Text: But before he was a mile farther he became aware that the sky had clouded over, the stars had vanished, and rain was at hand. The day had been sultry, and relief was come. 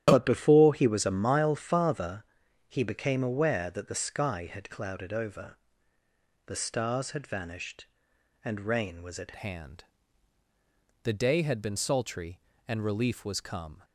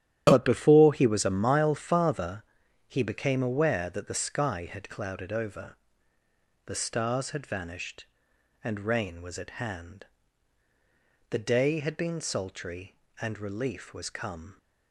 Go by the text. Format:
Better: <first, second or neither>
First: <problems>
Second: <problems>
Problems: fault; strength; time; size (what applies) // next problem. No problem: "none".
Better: second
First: starts louder than the rest; strong; until 1.0 s; 11 dB // pauses between "farther" and "he"; at 2.2 s; 0.44 s long // changes voice at "hand"; from 9.3 s on; 4.5 s long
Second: starts louder than the rest; strong; until 1.2 s; 11 dB // pauses between "farther" and "he"; at 2.4 s; 0.44 s long